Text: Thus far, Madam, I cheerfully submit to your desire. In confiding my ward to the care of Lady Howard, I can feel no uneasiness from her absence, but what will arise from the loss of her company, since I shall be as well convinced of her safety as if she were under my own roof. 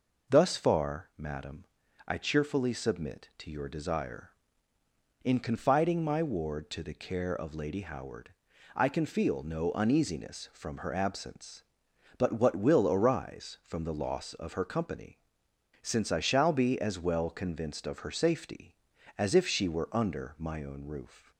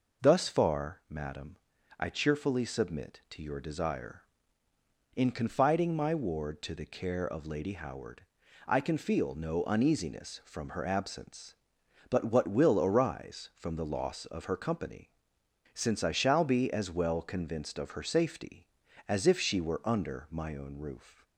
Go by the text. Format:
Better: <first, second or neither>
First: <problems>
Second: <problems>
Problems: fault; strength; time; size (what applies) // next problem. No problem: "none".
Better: neither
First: none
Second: none